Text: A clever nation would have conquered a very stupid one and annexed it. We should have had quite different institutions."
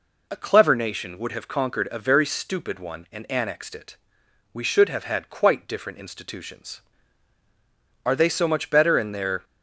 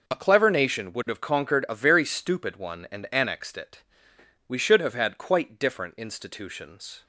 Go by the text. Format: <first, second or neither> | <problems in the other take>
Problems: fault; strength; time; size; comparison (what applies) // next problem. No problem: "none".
second | goes on to say "Are they so much better in their"; from 8.0 s on; 1.4 s long